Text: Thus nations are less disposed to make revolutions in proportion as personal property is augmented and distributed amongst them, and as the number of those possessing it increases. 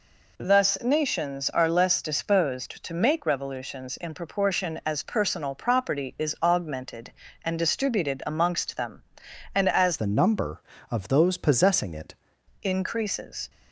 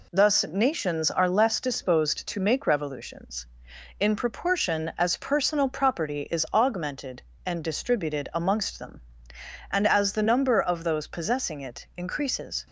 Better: second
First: changes voice from "the" to "it"; from 9.9 to 12.1 s; 2.2 s long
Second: none

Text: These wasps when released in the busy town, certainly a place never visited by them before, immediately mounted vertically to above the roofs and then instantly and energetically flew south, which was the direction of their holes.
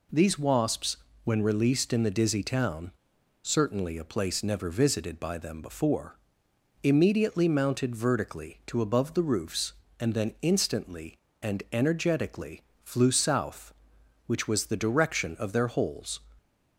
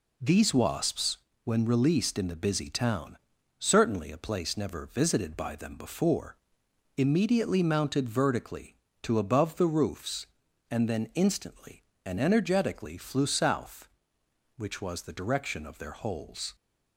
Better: second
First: pauses between "wasps" and "when"; slight; at 0.9 s; 0.28 s long // says "dizzy" for "busy"; at 2.1 s // pauses between "energetically" and "flew"; slight; at 12.6 s; 0.20 s long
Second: pauses between "wasps" and "when"; slight; at 1.1 s; 0.26 s long

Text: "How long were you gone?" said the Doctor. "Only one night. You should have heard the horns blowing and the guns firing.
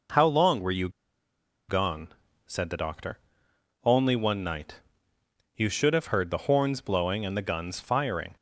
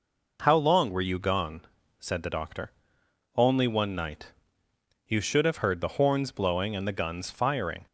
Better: second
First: pauses between "you" and "gone"; noticeable; at 0.8 s; 0.80 s long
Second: none

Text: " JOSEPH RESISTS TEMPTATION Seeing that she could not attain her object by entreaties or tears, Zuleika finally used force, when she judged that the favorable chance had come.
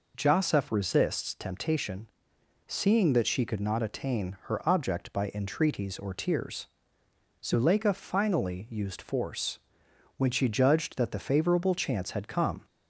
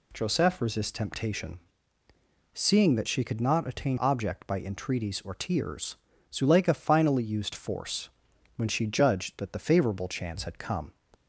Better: first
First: pauses between "TEMPTATION" and "Seeing"; noticeable; at 2.0 s; 0.58 s long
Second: pauses between "TEMPTATION" and "Seeing"; noticeable; at 1.5 s; 0.94 s long // skips "her"; at 3.9 s

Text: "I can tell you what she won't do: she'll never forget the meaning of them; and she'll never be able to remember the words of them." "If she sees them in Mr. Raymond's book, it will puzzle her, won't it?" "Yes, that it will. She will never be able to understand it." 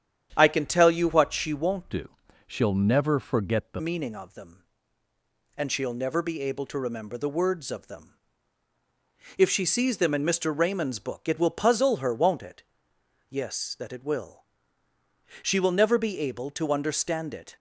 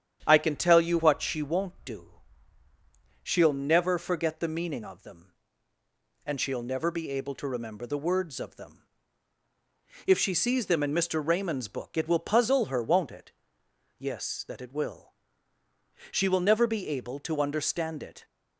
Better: second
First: starts louder than the rest; strong; until 1.3 s; 9 dB // changes voice from "do" to "the"; from 1.9 to 3.8 s; 1.9 s long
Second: starts louder than the rest; strong; until 1.2 s; 9 dB

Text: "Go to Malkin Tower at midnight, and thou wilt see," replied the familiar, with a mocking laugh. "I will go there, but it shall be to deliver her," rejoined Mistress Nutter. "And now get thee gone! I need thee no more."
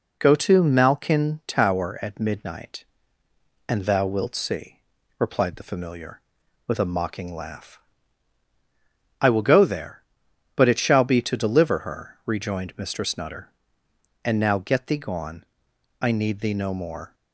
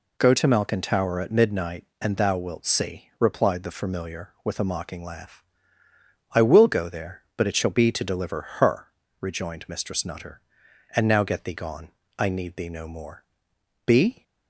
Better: first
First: none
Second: pauses between "deliver" and "her"; slight; at 8.4 s; 0.16 s long // goes on to say "Be"; slight; from 13.8 s on; 0.38 s long

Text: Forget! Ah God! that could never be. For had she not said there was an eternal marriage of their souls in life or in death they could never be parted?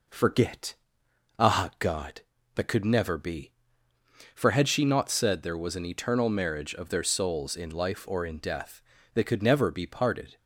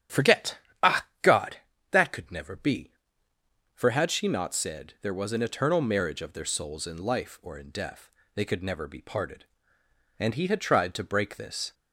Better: first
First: pauses between "death" and "they"; slight; at 8.8 s; 0.32 s long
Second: starts louder than the rest; strong; until 1.5 s; 9 dB // pauses between "Ah" and "God"; slight; at 1.0 s; 0.18 s long // pauses between "death" and "they"; slight; at 8.0 s; 0.24 s long // goes on to say "And he had tried to break this"; from 10.1 s on; 1.5 s long

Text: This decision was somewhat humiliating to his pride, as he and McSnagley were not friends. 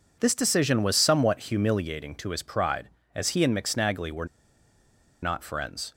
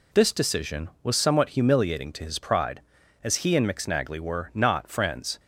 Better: second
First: pauses between "were" and "not"; noticeable; at 4.2 s; 0.96 s long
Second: none

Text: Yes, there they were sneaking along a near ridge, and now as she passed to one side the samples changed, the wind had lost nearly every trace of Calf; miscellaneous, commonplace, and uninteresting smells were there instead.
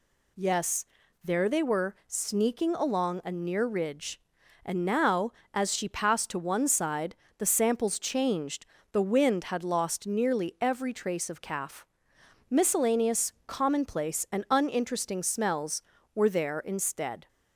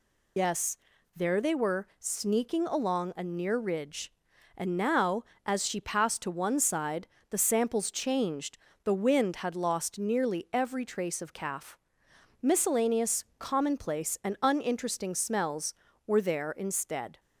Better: first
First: pauses between "side" and "the"; slight; at 7.1 s; 0.22 s long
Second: loses the start of "Yes"; at 0.3 s; 85 ms // pauses between "side" and "the"; slight; at 7.0 s; 0.22 s long

